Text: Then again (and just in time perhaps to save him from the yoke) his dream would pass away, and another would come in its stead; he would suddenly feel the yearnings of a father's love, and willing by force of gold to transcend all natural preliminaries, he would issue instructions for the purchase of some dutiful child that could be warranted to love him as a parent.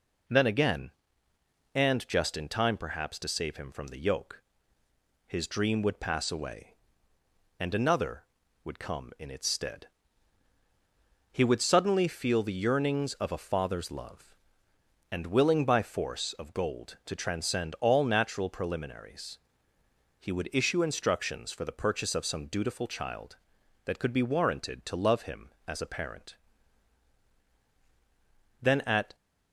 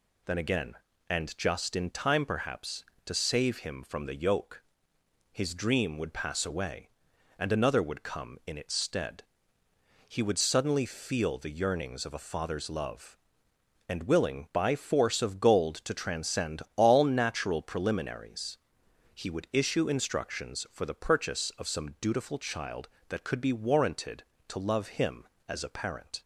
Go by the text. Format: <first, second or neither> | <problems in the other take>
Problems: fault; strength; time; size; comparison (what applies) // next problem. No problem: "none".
second | goes on to say "Then at"; from 28.6 s on; 0.52 s long